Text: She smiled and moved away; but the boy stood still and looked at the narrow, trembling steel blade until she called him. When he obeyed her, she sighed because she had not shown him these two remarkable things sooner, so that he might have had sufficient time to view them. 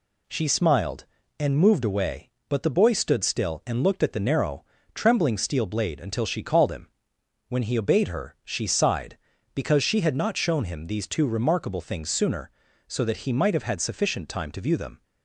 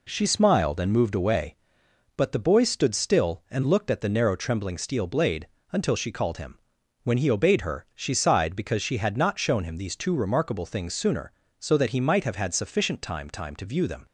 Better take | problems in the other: first | pauses between "blade" and "until"; slight; at 5.4 s; 0.22 s long // says "time" twice; at 13.2 s

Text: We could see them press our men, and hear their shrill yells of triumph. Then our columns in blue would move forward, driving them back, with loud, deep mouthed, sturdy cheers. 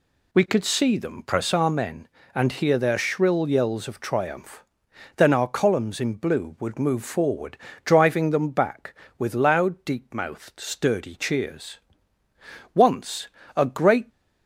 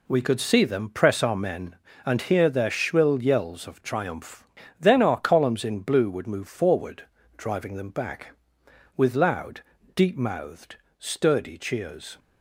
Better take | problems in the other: second | goes on to say "Once a great"; from 12.7 s on; 1.3 s long

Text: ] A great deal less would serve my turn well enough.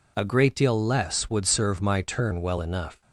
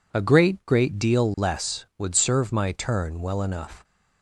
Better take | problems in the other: first | says "great" twice; at 0.6 s

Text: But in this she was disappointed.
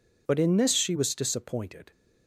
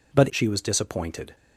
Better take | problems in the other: first | skips "in this"; at 0.2 s

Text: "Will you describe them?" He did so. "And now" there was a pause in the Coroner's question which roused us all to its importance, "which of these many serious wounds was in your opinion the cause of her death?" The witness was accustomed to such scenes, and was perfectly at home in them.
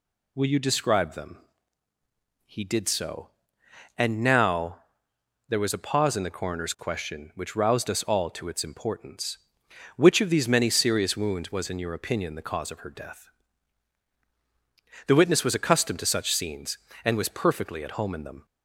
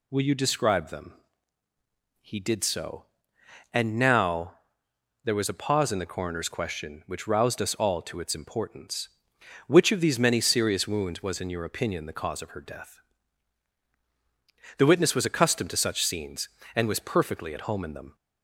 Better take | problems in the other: neither | pauses between "now" and "there"; noticeable; the same in both

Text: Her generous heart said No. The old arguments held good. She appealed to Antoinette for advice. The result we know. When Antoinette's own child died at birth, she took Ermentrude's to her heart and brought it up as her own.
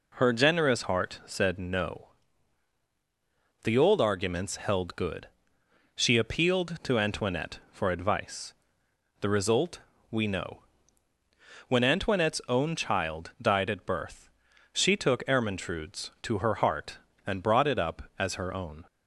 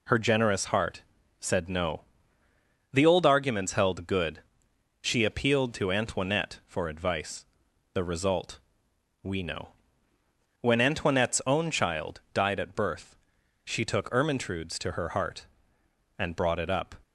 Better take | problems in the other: first | pauses between "heart" and "said"; slight; at 1.0 s; 0.36 s long // pauses between "result" and "we"; noticeable; at 8.5 s; 0.64 s long; slight in the first // stops before "as her own"; at 17.0 s

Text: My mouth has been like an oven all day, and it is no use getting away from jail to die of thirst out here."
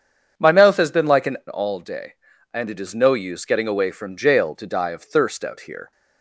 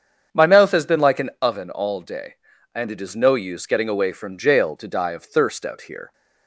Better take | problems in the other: second | starts louder than the rest; strong; until 1.5 s; 7.5 dB; strong in the second // skips "oven"; at 1.4 s

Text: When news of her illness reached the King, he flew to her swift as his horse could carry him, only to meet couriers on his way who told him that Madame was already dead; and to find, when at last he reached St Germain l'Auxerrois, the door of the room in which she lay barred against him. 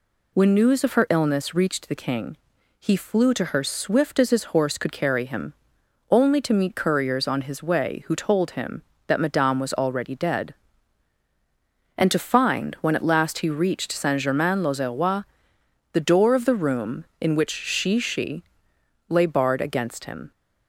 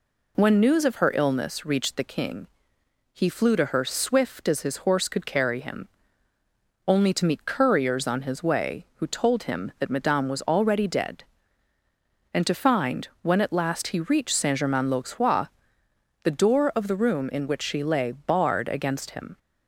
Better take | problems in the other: second | says "she" twice; at 17.9 s

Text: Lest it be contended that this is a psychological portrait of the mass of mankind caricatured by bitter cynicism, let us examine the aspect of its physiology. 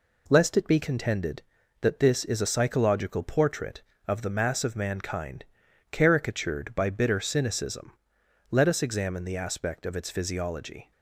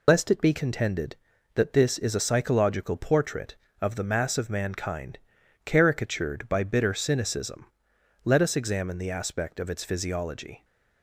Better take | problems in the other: first | loses the start of "Lest"; at 0.0 s; 85 ms // pauses between "mankind" and "caricatured"; noticeable; at 5.1 s; 0.48 s long; noticeable in the first

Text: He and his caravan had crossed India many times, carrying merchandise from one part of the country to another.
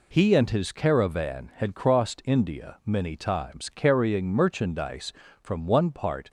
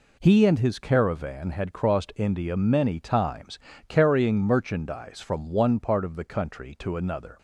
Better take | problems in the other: second | stops before "of the country to another"; at 6.2 s

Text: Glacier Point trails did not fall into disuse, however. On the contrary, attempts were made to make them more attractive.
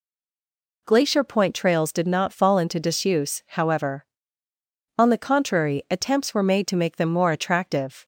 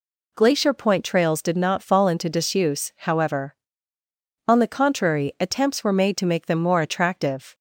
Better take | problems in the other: second | stays silent before the first word; slight; until 0.8 s; 0.8 s long

